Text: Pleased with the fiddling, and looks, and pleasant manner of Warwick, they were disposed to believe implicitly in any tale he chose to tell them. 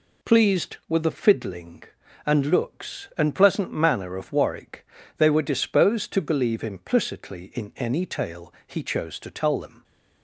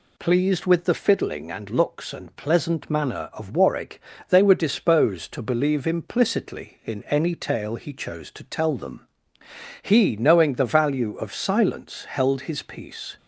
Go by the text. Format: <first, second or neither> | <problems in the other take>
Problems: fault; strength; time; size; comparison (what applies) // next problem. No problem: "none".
first | goes on to say "He knowing the value of silence held his peace"; strong; from 9.8 s on; 3.3 s long